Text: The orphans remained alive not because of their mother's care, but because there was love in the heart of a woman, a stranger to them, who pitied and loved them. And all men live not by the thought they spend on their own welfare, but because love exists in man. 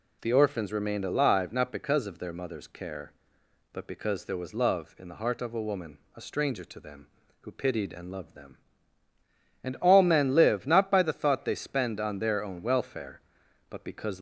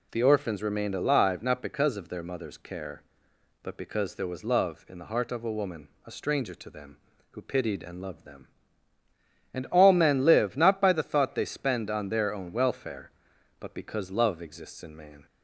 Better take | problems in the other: second | stops before "love exists in man"; at 14.1 s

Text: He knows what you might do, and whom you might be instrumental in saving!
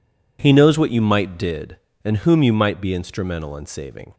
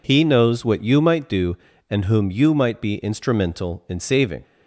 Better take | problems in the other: second | says "did" for "do"; at 1.3 s

